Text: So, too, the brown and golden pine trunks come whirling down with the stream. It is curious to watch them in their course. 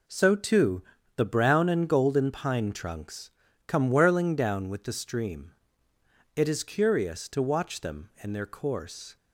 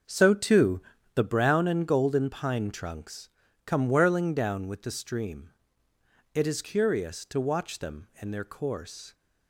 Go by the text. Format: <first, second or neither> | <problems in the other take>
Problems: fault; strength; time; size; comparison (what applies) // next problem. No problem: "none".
first | starts louder than the rest; until 1.3 s; 6 dB // pauses between "trunks" and "come"; at 3.2 s; 0.38 s long; also in the first